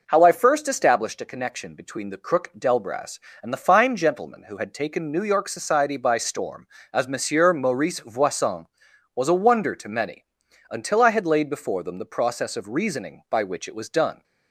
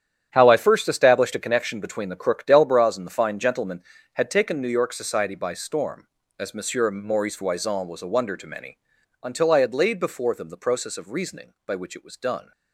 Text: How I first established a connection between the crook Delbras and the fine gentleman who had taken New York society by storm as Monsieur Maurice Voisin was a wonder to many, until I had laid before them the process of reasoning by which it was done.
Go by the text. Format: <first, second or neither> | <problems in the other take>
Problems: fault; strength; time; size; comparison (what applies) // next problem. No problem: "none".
first | starts louder than the rest; strong; until 1.3 s; 10 dB // skips "who"; at 3.9 s